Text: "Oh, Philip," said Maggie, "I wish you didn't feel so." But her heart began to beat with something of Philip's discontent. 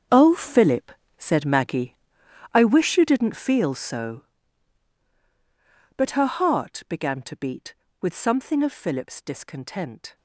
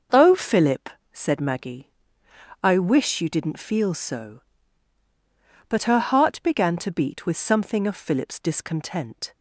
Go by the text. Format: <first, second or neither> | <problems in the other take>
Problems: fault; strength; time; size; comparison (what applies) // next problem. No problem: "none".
second | gets quieter; strong; throughout; 15 dB